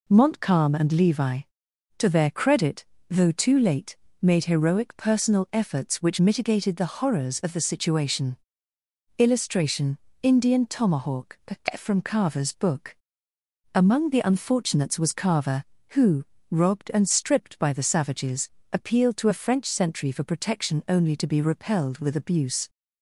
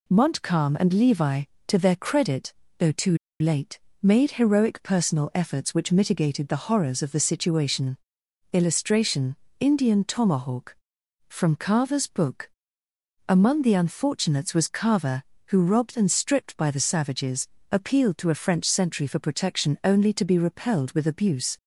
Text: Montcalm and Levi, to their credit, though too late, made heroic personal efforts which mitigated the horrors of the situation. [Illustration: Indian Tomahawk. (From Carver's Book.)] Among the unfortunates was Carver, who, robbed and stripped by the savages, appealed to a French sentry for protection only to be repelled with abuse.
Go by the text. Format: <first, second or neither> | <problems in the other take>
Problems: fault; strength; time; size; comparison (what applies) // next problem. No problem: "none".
first | pauses between "too" and "late"; slight; at 3.1 s; 0.23 s long